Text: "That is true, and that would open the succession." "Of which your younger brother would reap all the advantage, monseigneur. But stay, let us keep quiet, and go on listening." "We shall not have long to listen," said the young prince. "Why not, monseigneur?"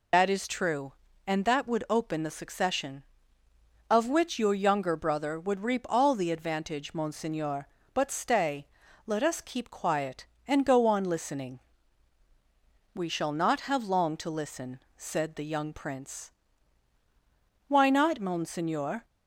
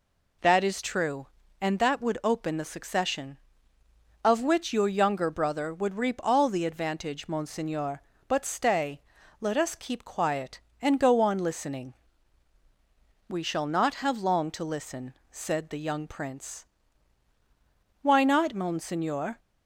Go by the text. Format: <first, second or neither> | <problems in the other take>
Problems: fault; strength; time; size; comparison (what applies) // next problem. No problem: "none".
second | loses the start of "That"; at 0.1 s; 70 ms